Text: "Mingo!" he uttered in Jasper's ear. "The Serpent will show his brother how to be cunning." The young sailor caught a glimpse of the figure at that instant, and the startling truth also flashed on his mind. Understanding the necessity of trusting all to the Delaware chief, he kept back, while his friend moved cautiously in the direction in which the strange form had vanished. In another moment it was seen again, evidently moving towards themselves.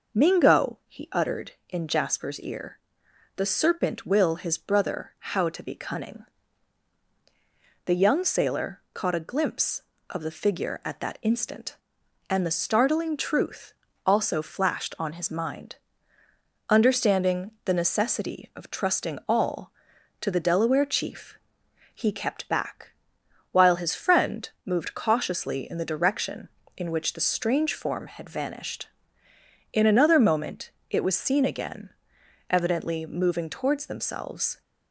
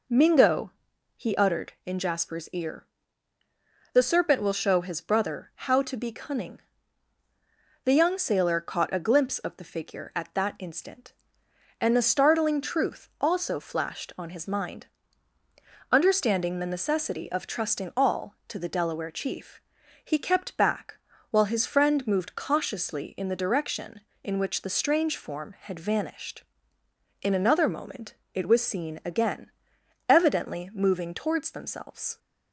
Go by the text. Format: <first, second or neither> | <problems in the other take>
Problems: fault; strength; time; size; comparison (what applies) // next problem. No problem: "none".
second | skips "show"; at 4.3 s // pauses between "truth" and "also"; slight; at 13.7 s; 0.32 s long // pauses between "friend" and "moved"; slight; at 24.4 s; 0.16 s long // pauses between "moment" and "it"; slight; at 30.6 s; 0.20 s long; slight in the second